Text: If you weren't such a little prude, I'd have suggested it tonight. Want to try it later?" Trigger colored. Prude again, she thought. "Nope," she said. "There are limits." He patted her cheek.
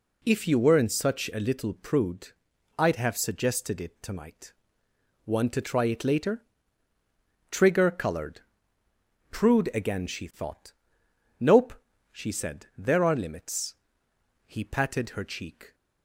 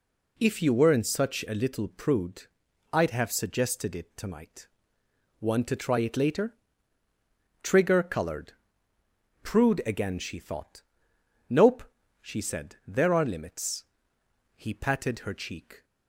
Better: neither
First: none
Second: none

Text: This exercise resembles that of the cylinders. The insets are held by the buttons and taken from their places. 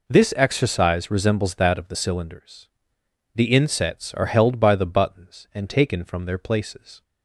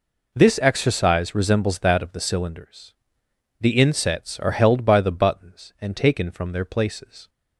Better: neither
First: none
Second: none

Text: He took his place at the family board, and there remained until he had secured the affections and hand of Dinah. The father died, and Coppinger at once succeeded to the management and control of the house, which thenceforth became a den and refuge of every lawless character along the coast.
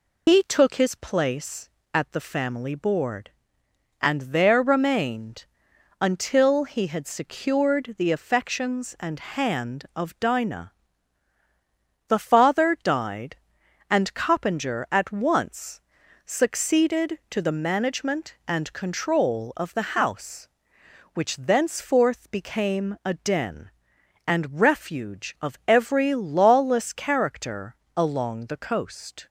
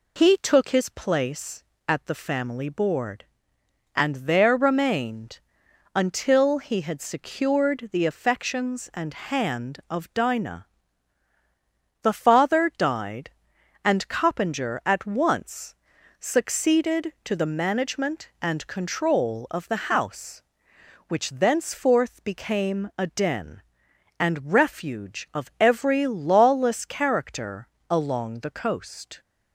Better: second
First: loses the start of "He"; at 0.2 s; 55 ms // pauses between "remained" and "until"; noticeable; at 5.4 s; 0.54 s long // pauses between "once" and "succeeded"; at 15.8 s; 0.44 s long // pauses between "character" and "along"; slight; at 27.7 s; 0.22 s long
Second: pauses between "remained" and "until"; noticeable; at 5.4 s; 0.54 s long // pauses between "once" and "succeeded"; at 15.7 s; 0.44 s long // pauses between "character" and "along"; slight; at 27.6 s; 0.24 s long

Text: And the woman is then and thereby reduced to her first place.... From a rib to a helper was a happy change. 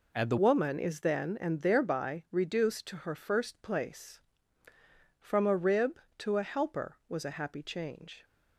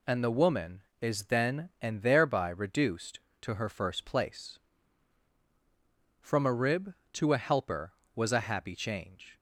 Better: second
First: changes voice at "woman"; from 0.3 s on; 7.9 s long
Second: none

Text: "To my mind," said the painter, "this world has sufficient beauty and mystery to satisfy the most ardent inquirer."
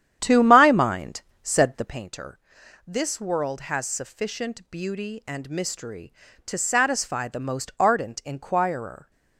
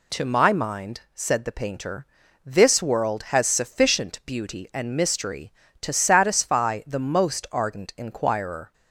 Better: second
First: starts louder than the rest; strong; until 2.1 s; 10 dB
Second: none

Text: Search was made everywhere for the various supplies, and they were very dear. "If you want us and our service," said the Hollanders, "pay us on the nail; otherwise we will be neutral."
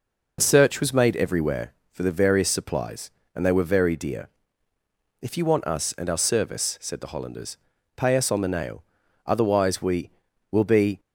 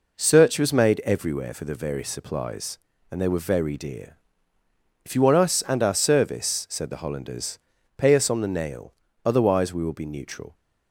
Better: second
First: stops before "neutral"; at 10.9 s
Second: none

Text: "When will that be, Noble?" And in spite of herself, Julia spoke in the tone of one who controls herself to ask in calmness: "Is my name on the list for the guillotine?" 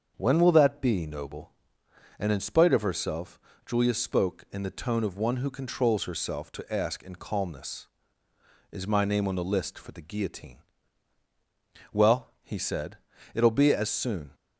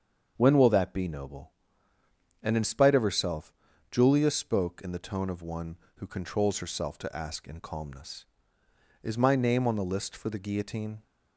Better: second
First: starts louder than the rest; until 1.1 s; 6.5 dB // goes on to say "Well he said it'll be as soon"; strong; from 11.9 s on; 2.4 s long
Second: starts louder than the rest; until 1.3 s; 7 dB

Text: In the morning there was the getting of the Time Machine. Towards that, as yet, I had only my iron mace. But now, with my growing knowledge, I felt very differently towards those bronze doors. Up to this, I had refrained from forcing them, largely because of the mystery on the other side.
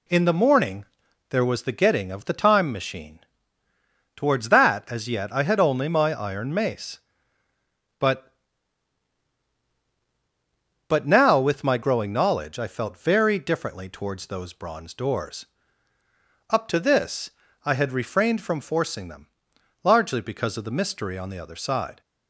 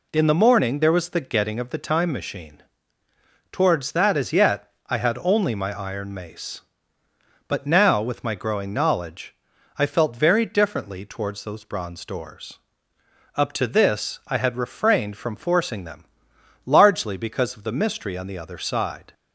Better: second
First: pauses between "morning" and "there"; noticeable; at 0.8 s; 0.46 s long // says "But" twice; at 10.8 s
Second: none

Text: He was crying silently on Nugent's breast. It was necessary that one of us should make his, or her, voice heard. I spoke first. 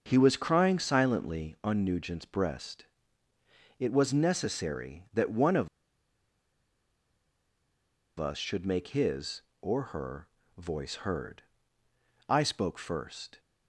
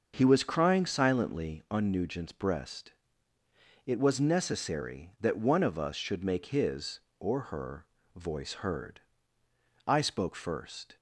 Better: second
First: starts louder than the rest; until 1.0 s; 6.5 dB // pauses between "of" and "us"; strong; at 5.6 s; 2.4 s long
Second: starts louder than the rest; until 1.1 s; 6 dB

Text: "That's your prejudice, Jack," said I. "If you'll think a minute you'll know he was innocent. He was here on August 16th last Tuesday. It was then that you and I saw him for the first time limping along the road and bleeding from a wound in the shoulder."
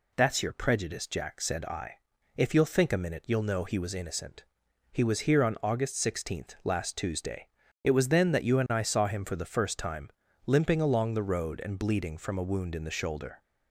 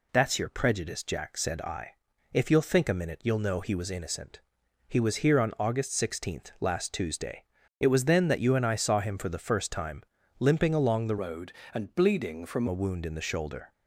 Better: first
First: pauses between "time" and "limping"; at 10.0 s; 0.38 s long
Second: pauses between "time" and "limping"; at 10.0 s; 0.38 s long // changes voice from "road" to "from"; from 11.2 to 12.6 s; 1.4 s long

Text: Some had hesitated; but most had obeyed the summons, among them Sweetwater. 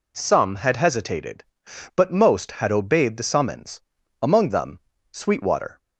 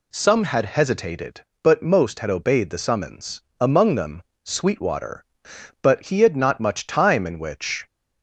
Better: first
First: pauses between "them" and "Sweetwater"; slight; at 4.7 s; 0.32 s long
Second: pauses between "them" and "Sweetwater"; slight; at 4.2 s; 0.22 s long // goes on to say "But he had not much time in which"; strong; from 5.8 s on; 2.0 s long

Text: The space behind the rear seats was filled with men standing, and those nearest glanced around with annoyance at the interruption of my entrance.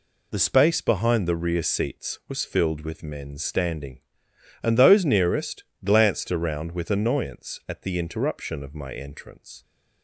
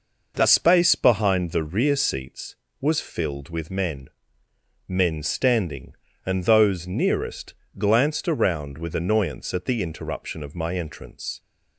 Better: first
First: pauses between "nearest" and "glanced"; slight; at 5.6 s; 0.22 s long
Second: says "men" twice; at 4.8 s // pauses between "nearest" and "glanced"; slight; at 7.5 s; 0.24 s long

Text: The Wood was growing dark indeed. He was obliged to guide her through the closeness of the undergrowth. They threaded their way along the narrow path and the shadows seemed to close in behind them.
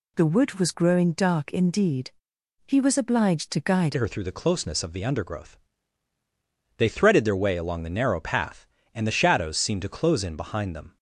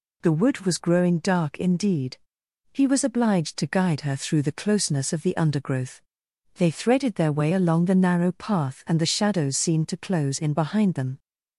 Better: second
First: changes voice at "her"; from 3.9 s on; 7.0 s long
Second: none

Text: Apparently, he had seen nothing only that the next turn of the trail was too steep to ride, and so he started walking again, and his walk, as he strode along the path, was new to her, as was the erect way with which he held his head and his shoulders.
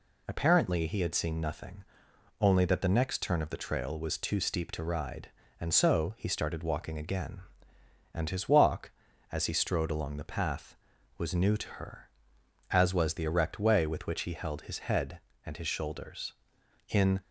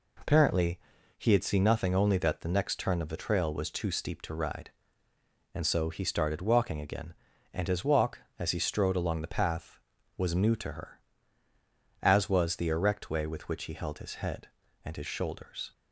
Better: second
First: pauses between "nothing" and "only"; noticeable; at 1.8 s; 0.56 s long // goes on to say "In"; slight; from 16.8 s on; 0.32 s long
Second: none

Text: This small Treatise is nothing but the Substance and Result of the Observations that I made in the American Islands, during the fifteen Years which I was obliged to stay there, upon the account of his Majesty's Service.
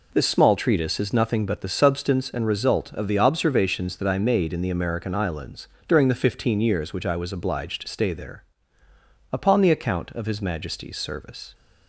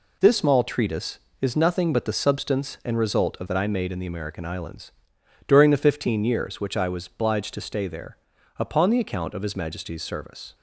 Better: first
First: none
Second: skips "the Observations"; at 3.4 s

